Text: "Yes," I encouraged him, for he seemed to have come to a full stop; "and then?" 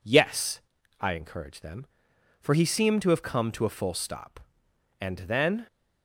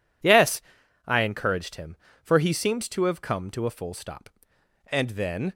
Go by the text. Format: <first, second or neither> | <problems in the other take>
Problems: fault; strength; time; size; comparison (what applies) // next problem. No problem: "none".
second | says "them" for "him"; at 1.6 s